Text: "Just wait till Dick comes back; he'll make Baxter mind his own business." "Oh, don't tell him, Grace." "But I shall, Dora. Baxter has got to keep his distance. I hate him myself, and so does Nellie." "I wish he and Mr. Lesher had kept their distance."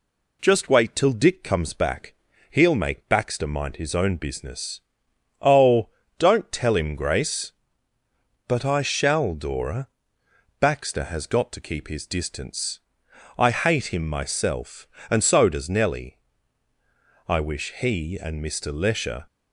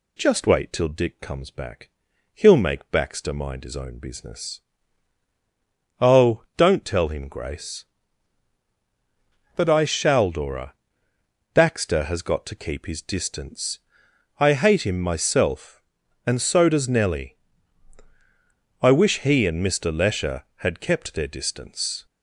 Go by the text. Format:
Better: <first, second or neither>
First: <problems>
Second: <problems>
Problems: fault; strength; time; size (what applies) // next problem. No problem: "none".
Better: second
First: stops before "had kept their distance"; at 19.2 s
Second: none